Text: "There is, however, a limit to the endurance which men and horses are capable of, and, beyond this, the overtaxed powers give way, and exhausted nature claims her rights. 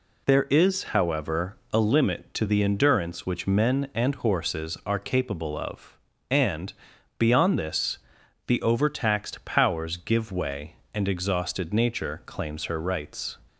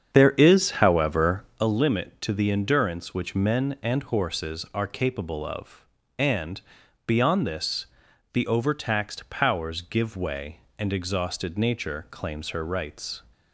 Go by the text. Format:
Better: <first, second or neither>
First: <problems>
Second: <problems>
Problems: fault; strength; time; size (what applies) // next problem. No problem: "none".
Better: first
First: none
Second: starts louder than the rest; strong; until 1.6 s; 8 dB